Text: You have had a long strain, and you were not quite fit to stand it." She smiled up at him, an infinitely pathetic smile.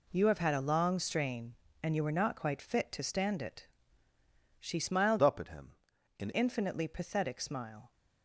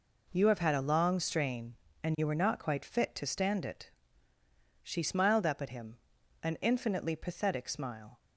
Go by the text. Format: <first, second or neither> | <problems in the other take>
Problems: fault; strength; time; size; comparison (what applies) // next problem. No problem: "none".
second | changes voice from "up" to "an"; from 5.2 to 6.3 s; 1.1 s long